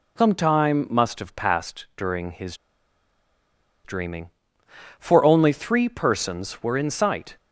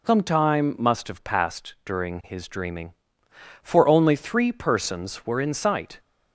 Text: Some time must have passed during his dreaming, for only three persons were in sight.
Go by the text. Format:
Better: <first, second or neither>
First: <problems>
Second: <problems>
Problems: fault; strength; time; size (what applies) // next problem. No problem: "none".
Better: second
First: pauses between "his" and "dreaming"; strong; at 2.5 s; 1.2 s long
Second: none